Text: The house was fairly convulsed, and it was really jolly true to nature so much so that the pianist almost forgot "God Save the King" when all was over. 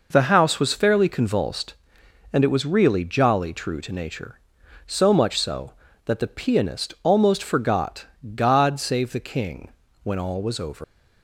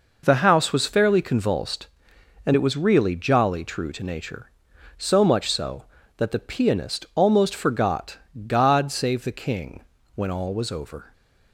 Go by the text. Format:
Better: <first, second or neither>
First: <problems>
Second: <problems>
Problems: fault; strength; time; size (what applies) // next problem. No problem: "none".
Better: second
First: pauses between "forgot" and "God"; slight; at 8.0 s; 0.28 s long // pauses between "King" and "when"; slight; at 9.6 s; 0.34 s long // leaves "over" unfinished; at 10.8 s; 165 ms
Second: pauses between "forgot" and "God"; slight; at 8.1 s; 0.28 s long // pauses between "King" and "when"; slight; at 9.8 s; 0.34 s long